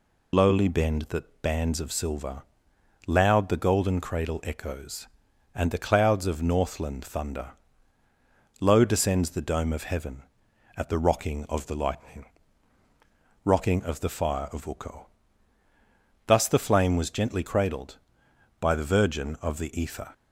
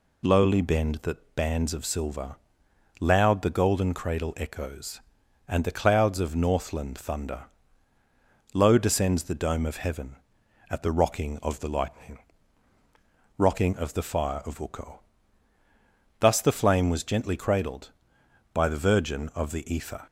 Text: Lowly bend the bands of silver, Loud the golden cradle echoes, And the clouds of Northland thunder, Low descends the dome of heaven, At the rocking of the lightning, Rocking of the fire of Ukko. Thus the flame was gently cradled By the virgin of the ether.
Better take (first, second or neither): second